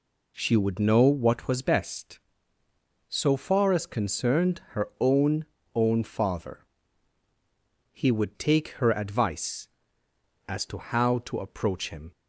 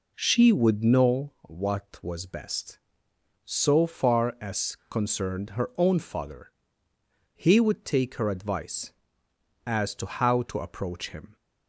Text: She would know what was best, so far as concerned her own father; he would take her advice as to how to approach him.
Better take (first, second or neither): second